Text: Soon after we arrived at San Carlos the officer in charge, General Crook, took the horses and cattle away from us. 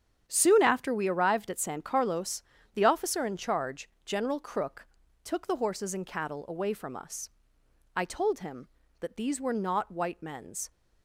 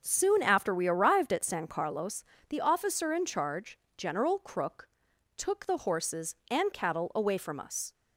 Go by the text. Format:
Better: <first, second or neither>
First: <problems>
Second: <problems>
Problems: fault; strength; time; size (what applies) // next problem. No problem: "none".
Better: second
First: starts louder than the rest; strong; until 1.2 s; 9 dB // pauses between "Carlos" and "the"; slight; at 2.4 s; 0.32 s long // goes on to say "I told him that these were not white men's"; strong; from 7.9 s on; 2.7 s long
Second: starts louder than the rest; noticeable; until 1.0 s; 6 dB // pauses between "Carlos" and "the"; slight; at 2.2 s; 0.26 s long